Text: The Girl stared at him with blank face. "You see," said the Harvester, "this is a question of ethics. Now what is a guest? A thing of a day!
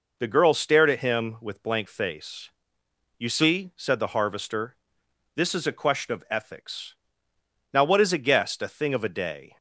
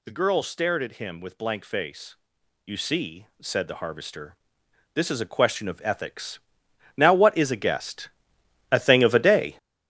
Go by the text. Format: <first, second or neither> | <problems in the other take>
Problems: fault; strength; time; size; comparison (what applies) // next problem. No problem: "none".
first | gets louder; strong; throughout; 9 dB